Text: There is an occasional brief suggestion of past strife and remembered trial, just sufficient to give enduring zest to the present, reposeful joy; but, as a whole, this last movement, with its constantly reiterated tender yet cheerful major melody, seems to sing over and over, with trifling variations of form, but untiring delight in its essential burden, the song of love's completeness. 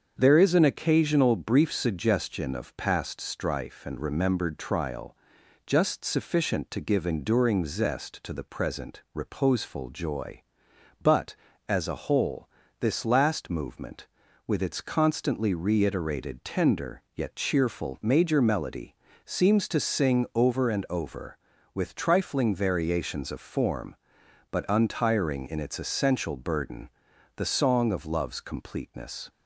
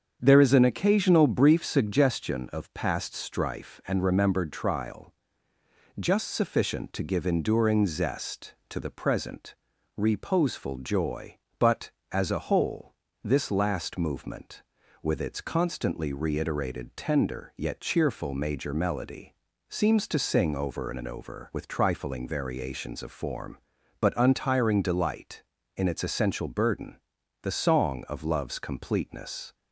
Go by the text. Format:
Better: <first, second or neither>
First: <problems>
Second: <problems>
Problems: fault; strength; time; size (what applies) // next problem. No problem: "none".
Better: second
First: starts louder than the rest; until 1.2 s; 7 dB // skips "delight"; at 25.4 s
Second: starts louder than the rest; strong; until 1.2 s; 7.5 dB